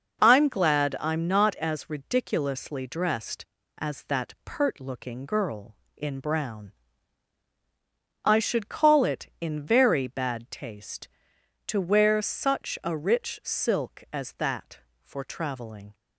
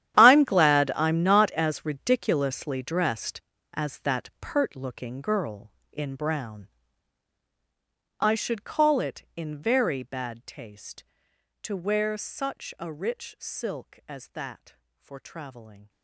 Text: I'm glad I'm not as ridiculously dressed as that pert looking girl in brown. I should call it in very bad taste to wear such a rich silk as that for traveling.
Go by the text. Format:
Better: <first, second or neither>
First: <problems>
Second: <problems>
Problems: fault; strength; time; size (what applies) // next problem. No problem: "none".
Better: first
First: none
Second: gets quieter; strong; throughout; 17.5 dB